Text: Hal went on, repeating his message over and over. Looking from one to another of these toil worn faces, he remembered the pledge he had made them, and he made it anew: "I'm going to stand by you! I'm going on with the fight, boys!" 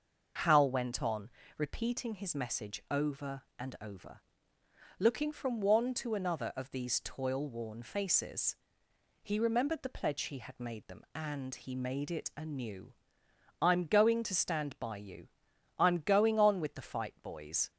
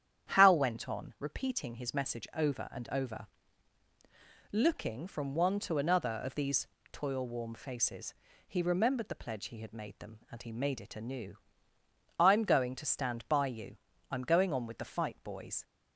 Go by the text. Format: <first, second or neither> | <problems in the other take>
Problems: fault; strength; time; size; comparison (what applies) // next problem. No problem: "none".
first | starts louder than the rest; strong; until 1.3 s; 9.5 dB // pauses between "these" and "toil"; slight; at 6.6 s; 0.26 s long // says "warm" for "worn"; at 7.2 s